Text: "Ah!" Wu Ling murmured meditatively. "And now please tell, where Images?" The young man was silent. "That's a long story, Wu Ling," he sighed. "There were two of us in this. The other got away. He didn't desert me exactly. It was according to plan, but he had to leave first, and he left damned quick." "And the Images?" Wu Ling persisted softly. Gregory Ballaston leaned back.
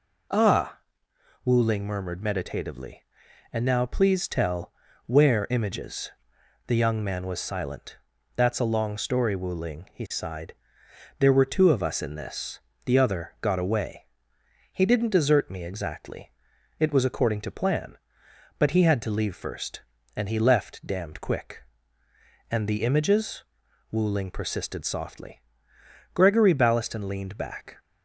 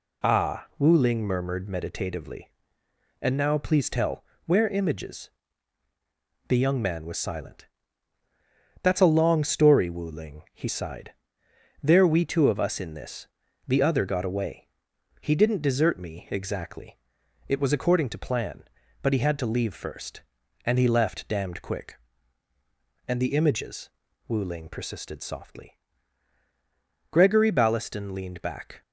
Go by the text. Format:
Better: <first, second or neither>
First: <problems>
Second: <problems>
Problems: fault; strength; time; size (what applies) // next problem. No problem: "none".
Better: first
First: none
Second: says "we" for "were"; at 12.0 s